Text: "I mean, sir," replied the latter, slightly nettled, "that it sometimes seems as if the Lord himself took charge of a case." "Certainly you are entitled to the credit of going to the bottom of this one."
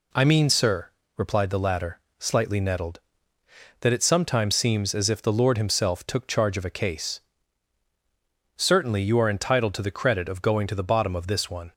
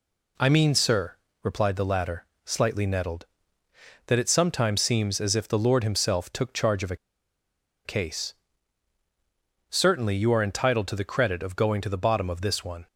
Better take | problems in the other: first | pauses between "a" and "case"; noticeable; at 6.9 s; 0.89 s long

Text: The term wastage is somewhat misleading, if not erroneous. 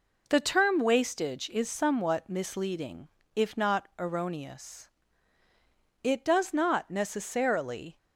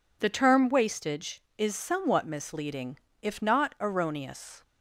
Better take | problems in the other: second | goes on to say "It does not necessarily"; strong; from 6.0 s on; 1.9 s long

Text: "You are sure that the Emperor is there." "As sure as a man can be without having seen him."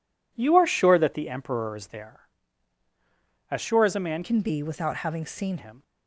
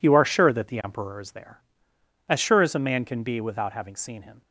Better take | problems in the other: second | changes voice from "can" to "seen"; from 4.2 to 5.5 s; 1.3 s long

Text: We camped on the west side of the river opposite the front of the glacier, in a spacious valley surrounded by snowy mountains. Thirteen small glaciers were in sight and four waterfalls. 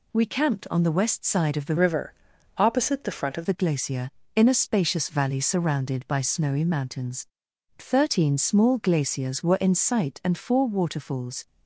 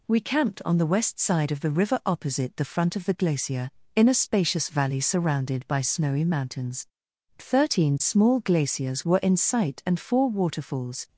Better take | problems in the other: second | changes voice from "river" to "of"; from 1.7 to 3.4 s; 1.7 s long // pauses between "river" and "opposite"; noticeable; at 2.1 s; 0.46 s long

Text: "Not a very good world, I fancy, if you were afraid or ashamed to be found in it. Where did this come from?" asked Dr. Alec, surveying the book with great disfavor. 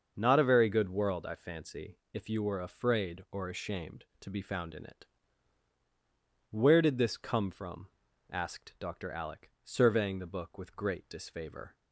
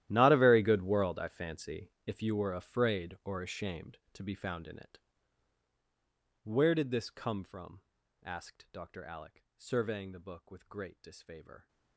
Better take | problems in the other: first | gets quieter; strong; throughout; 20.5 dB // starts louder than the rest; strong; until 1.1 s; 13 dB; also in the first

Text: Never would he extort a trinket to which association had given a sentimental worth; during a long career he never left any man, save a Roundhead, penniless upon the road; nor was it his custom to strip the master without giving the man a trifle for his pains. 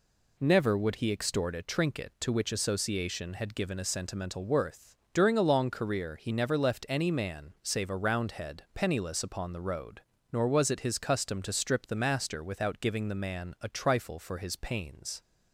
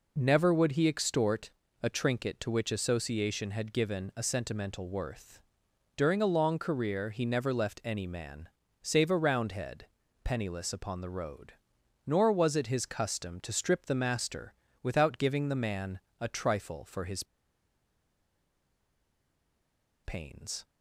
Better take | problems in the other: first | pauses between "extort" and "a"; slight; at 1.5 s; 0.32 s long // pauses between "master" and "without"; slight; at 14.5 s; 0.26 s long // pauses between "man" and "a"; slight; at 15.9 s; 0.20 s long // pauses between "his" and "pains"; strong; at 17.2 s; 2.8 s long

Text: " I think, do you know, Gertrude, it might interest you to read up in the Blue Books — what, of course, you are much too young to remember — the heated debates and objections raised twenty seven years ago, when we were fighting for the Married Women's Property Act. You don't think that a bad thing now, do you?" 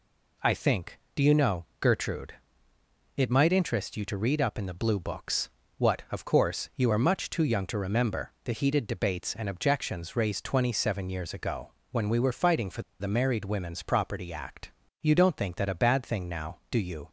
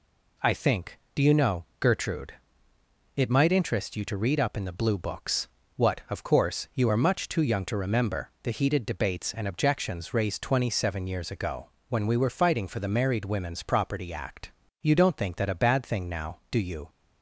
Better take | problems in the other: second | pauses between "for" and "the"; slight; at 12.8 s; 0.18 s long

